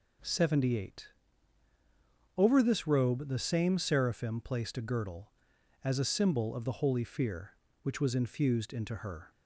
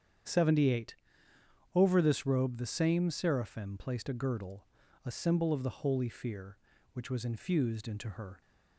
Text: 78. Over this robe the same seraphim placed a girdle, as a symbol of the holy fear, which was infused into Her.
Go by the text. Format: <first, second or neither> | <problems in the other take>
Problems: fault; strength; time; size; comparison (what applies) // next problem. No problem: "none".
first | starts louder than the rest; strong; until 2.0 s; 8.5 dB // skips "as"; at 4.8 s